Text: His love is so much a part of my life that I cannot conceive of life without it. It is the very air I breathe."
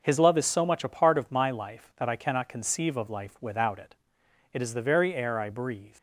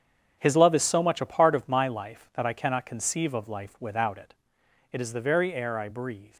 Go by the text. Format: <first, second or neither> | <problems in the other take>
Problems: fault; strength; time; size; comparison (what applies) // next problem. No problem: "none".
first | gets quieter; strong; throughout; 10.5 dB